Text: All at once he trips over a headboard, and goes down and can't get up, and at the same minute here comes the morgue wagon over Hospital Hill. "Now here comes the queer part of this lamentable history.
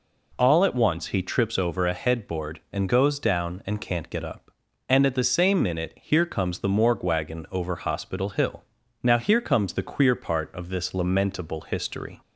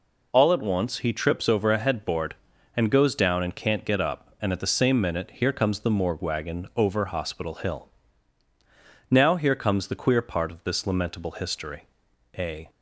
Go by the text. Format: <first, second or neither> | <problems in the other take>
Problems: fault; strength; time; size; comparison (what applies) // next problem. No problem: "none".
first | goes on to say "A"; slight; from 12.3 s on; 0.30 s long